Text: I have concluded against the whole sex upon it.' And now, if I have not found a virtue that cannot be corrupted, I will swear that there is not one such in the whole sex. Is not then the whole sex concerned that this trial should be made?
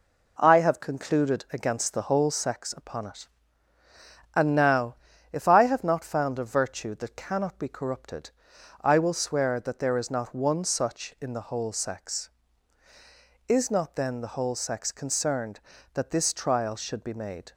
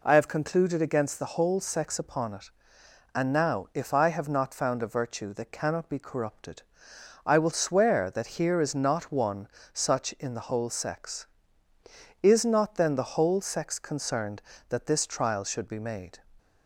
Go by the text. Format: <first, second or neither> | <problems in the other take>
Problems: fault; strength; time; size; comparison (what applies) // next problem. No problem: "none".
first | says "here" for "there"; at 8.4 s // pauses between "one" and "such"; slight; at 9.4 s; 0.28 s long